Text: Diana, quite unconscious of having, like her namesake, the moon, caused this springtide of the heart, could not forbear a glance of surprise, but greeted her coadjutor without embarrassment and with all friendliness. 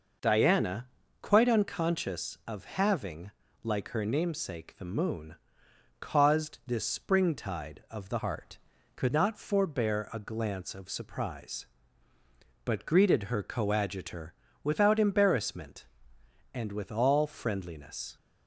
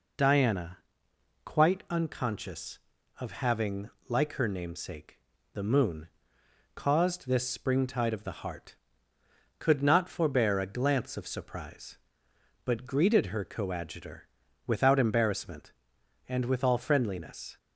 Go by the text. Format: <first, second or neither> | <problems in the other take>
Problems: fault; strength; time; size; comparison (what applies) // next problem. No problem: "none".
second | changes voice from "heart" to "could"; from 8.1 to 9.1 s; 1.0 s long // pauses between "coadjutor" and "without"; slight; at 14.3 s; 0.30 s long; also in the second